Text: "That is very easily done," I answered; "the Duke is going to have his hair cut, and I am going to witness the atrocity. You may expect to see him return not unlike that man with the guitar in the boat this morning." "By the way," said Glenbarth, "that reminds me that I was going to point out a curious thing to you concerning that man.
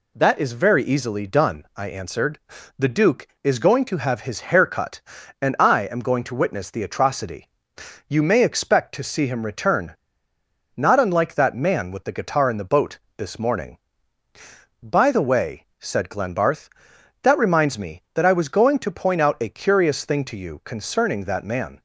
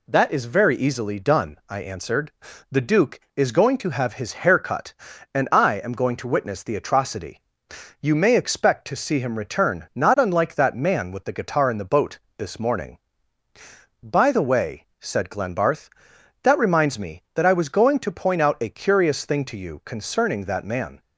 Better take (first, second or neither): second